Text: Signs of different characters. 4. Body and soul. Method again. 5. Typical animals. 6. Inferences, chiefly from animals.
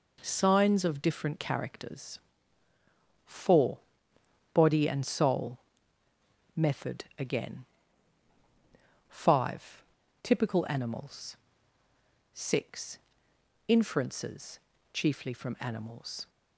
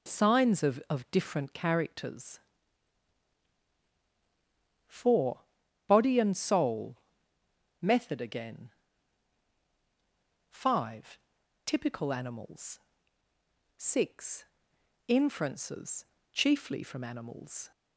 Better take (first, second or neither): first